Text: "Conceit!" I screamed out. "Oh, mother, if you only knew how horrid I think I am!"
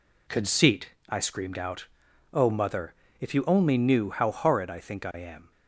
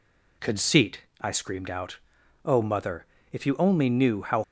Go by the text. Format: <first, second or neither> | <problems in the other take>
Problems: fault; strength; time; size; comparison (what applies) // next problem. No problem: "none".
first | stops before "horrid I think I am"; at 4.4 s